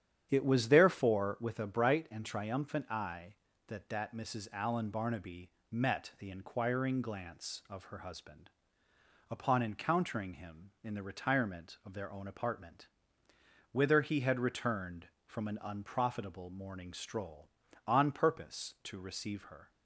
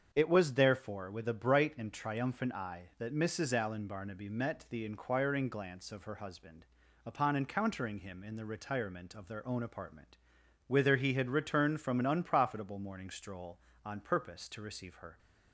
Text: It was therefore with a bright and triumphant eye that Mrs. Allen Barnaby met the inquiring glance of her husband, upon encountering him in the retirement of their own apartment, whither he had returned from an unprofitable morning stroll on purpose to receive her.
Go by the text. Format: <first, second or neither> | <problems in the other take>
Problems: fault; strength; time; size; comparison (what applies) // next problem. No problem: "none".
second | starts louder than the rest; strong; until 1.3 s; 9.5 dB; strong in the second // says "that" twice; at 3.8 s // pauses between "Barnaby" and "met"; slight; at 5.5 s; 0.20 s long